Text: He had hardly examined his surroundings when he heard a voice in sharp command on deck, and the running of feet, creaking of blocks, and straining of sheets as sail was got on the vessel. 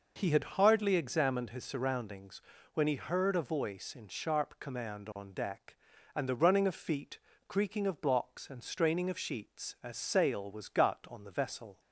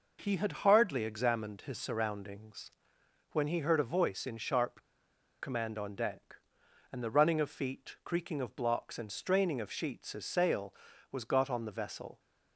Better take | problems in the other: first | pauses between "surroundings" and "when"; noticeable; at 2.7 s; 0.60 s long; slight in the first // pauses between "sharp" and "command"; noticeable; at 4.8 s; 0.57 s long

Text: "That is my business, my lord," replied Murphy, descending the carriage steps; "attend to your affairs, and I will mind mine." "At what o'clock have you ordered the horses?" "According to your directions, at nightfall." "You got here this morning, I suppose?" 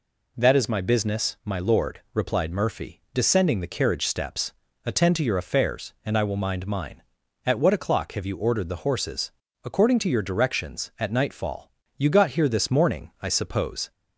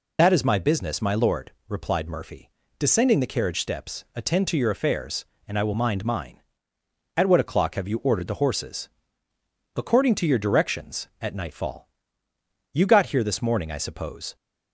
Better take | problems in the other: first | loses the start of "That"; at 0.1 s; 35 ms

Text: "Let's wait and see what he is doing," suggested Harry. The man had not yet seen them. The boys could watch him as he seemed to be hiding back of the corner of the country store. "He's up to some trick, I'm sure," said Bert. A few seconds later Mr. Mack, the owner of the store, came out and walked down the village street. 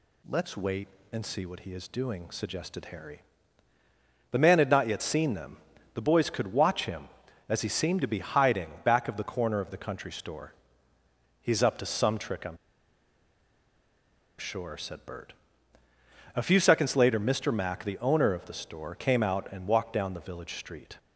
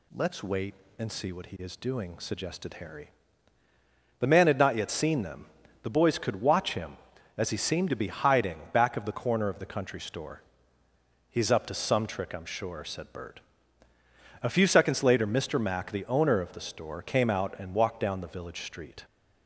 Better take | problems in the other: second | pauses between "I'm" and "sure"; strong; at 12.5 s; 1.8 s long

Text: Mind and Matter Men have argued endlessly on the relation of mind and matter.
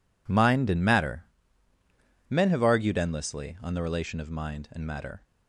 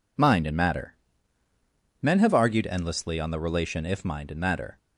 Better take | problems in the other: first | pauses between "Matter" and "Men"; at 0.9 s; 1.0 s long; also in the first // says "if" for "of"; at 3.8 s

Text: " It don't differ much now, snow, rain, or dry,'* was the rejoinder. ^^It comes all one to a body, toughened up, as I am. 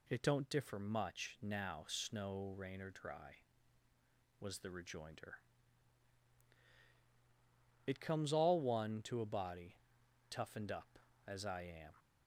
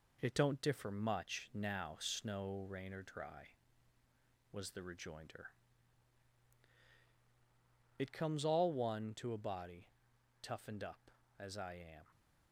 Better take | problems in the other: first | gets quieter; noticeable; throughout; 4 dB

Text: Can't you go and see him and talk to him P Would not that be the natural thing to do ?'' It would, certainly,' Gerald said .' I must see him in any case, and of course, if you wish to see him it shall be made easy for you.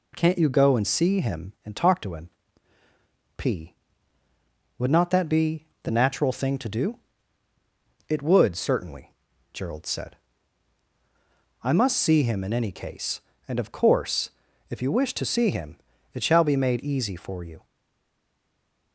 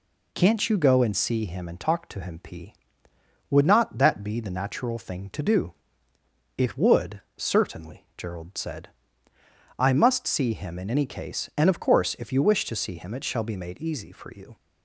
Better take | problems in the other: second | pauses between "him" and "P"; at 2.3 s; 1.0 s long // pauses between "be" and "the"; slight; at 5.6 s; 0.16 s long // pauses between "him" and "it"; slight; at 15.7 s; 0.34 s long // stays silent after the last word; noticeable; from 17.6 s on; 1.3 s long

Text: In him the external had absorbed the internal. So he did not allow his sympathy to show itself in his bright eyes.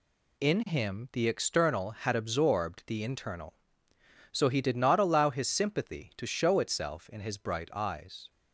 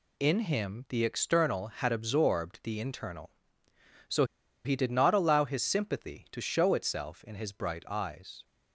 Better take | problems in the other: first | pauses between "So" and "he"; at 4.2 s; 0.40 s long

